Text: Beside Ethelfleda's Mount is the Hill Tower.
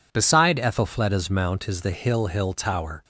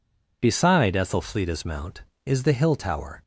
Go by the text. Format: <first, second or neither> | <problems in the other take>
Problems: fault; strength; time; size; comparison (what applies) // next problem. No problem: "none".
second | says "Hill" twice; at 2.2 s